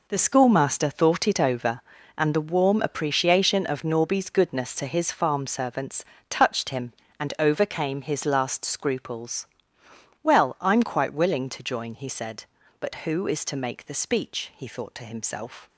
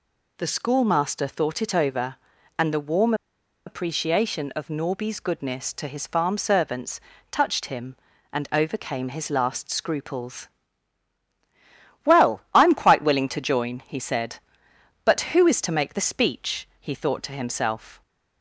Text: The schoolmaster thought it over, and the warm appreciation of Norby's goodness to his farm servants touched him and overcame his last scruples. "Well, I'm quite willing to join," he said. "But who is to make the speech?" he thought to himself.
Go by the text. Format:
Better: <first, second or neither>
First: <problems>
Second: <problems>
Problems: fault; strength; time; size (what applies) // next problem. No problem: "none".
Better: first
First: pauses between "servants" and "touched"; slight; at 6.0 s; 0.26 s long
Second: pauses between "warm" and "appreciation"; noticeable; at 3.1 s; 0.52 s long // pauses between "servants" and "touched"; slight; at 6.9 s; 0.32 s long